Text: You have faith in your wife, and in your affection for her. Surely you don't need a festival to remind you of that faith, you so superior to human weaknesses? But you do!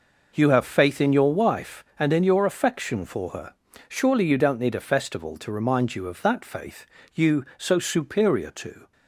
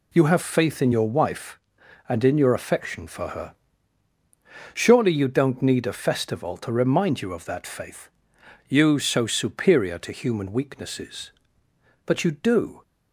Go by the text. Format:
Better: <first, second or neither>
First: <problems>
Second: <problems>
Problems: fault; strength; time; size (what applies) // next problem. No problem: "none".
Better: second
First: stops before "human weaknesses But you do"; at 8.9 s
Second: none